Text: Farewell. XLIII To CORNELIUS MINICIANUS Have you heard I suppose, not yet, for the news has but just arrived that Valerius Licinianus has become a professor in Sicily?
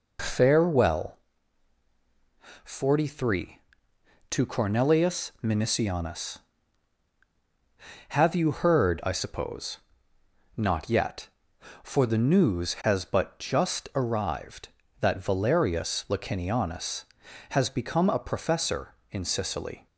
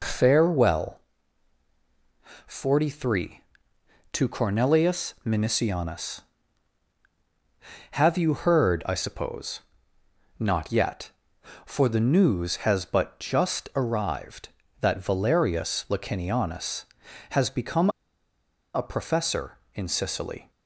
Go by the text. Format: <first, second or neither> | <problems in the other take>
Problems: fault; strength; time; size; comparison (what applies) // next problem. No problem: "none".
first | pauses between "become" and "a"; noticeable; at 17.8 s; 0.85 s long